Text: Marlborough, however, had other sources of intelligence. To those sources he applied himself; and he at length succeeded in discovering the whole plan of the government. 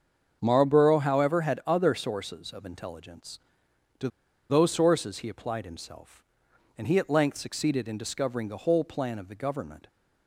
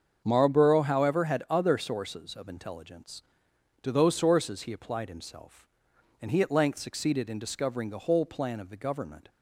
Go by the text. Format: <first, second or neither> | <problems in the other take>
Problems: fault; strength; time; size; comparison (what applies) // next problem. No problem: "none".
second | starts louder than the rest; until 1.4 s; 7 dB; also in the second // pauses between "To" and "those"; at 4.0 s; 0.41 s long